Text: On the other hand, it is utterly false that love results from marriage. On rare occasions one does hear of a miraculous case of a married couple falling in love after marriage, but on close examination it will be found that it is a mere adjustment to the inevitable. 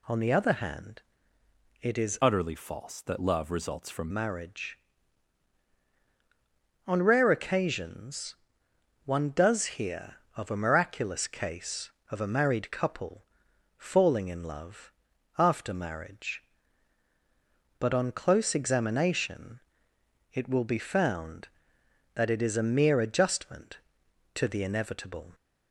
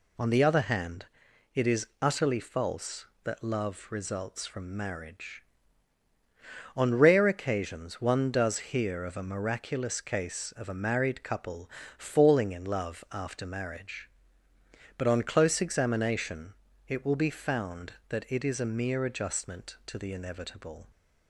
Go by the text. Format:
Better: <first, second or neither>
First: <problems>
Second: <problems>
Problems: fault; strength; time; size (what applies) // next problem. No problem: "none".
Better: second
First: changes voice from "utterly" to "from"; from 2.2 to 4.1 s; 1.9 s long // pauses between "occasions" and "one"; noticeable; at 8.3 s; 0.70 s long // pauses between "couple" and "falling"; noticeable; at 13.2 s; 0.54 s long // pauses between "love" and "after"; noticeable; at 14.9 s; 0.48 s long // pauses between "examination" and "it"; noticeable; at 19.6 s; 0.72 s long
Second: pauses between "couple" and "falling"; slight; at 11.6 s; 0.28 s long // pauses between "examination" and "it"; slight; at 16.5 s; 0.34 s long